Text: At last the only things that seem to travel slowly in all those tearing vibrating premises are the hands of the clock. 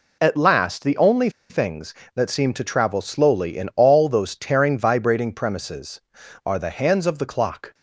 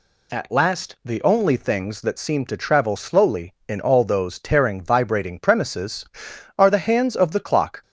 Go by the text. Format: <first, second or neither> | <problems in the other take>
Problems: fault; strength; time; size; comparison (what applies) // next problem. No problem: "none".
second | pauses between "only" and "things"; slight; at 1.3 s; 0.19 s long